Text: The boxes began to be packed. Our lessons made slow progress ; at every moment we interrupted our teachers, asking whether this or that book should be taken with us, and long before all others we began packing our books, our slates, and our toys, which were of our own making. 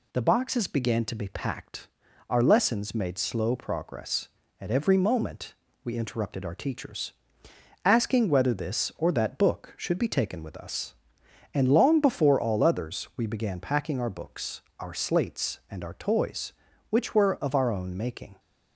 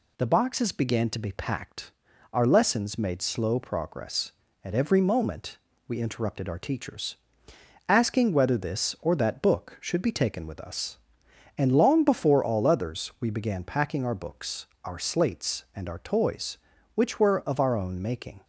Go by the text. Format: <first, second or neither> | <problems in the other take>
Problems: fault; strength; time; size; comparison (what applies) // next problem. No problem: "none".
neither | pauses between "moment" and "we"; slight; the same in both